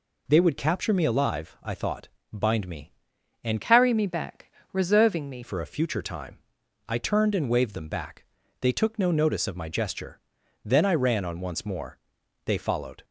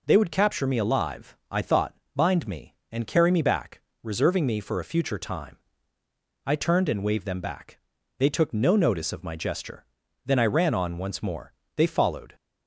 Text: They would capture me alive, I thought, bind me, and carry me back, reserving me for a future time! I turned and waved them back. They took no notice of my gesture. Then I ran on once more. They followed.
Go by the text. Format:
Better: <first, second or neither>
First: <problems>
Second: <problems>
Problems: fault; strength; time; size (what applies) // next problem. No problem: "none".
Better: second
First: changes voice from "carry" to "me"; from 3.6 to 5.4 s; 1.8 s long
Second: none